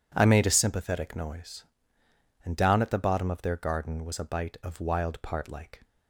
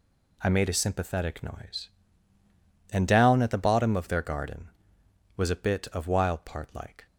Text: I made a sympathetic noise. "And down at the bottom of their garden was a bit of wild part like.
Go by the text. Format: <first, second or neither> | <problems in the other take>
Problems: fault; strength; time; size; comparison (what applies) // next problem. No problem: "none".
second | says "bite" for "bit"; at 4.2 s